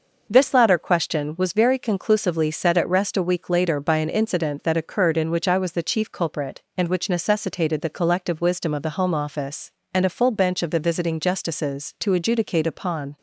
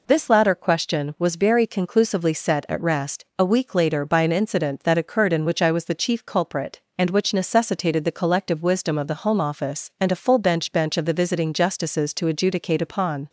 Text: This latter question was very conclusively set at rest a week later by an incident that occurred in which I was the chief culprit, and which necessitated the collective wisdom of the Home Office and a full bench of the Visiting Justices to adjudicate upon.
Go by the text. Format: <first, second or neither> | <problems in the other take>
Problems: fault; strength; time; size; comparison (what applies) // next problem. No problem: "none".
first | says "bench" twice; at 10.7 s